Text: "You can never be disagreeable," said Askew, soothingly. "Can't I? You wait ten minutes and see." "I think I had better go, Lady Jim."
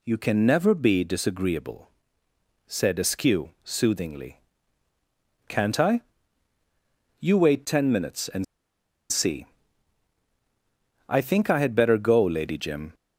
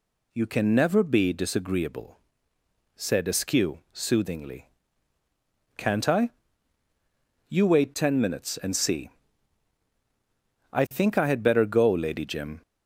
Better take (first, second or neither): second